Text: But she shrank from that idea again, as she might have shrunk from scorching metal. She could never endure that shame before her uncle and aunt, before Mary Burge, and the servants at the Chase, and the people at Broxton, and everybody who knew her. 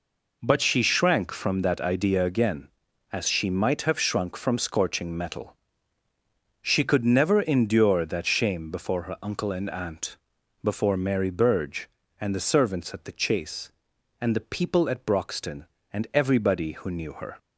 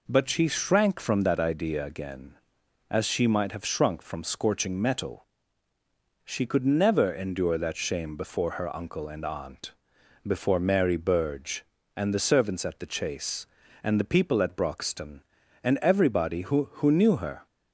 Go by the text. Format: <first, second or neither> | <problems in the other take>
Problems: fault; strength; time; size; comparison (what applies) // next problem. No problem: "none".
first | says "who" twice; at 16.7 s